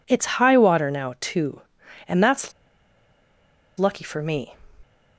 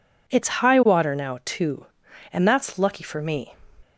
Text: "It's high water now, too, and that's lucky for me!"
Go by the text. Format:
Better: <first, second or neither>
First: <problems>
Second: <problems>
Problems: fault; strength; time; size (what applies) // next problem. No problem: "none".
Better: second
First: pauses between "that's" and "lucky"; strong; at 2.5 s; 1.2 s long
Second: none